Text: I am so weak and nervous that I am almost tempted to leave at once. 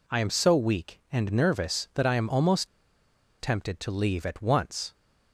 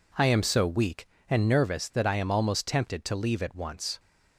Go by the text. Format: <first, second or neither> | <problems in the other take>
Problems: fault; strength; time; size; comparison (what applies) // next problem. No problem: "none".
second | pauses between "almost" and "tempted"; noticeable; at 2.6 s; 0.73 s long